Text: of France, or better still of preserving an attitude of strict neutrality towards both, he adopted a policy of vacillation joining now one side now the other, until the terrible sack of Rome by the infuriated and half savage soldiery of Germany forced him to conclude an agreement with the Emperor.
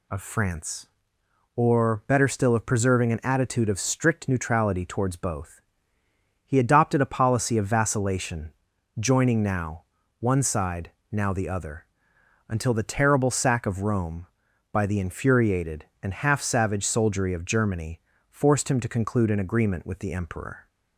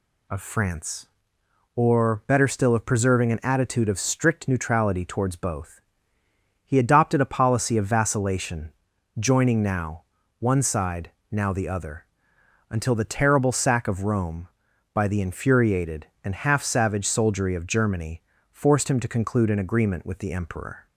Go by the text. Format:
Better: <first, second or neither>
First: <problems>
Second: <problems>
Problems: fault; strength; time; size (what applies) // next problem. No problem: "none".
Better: neither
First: pauses between "vacillation" and "joining"; noticeable; at 8.5 s; 0.46 s long // pauses between "now" and "one"; at 9.8 s; 0.38 s long // pauses between "side" and "now"; slight; at 10.9 s; 0.20 s long // pauses between "Germany" and "forced"; slight; at 18.0 s; 0.30 s long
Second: pauses between "vacillation" and "joining"; noticeable; at 8.7 s; 0.46 s long // pauses between "now" and "one"; at 10.0 s; 0.38 s long // pauses between "side" and "now"; slight; at 11.1 s; 0.20 s long // pauses between "Germany" and "forced"; slight; at 18.2 s; 0.30 s long